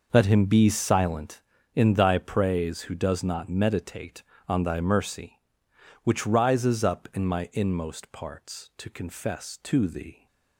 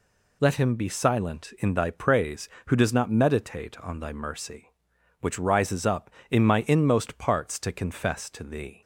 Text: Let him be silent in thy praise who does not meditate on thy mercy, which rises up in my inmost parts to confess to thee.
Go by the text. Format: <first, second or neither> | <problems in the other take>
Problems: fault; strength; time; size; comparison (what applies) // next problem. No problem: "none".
second | starts louder than the rest; noticeable; until 1.4 s; 6 dB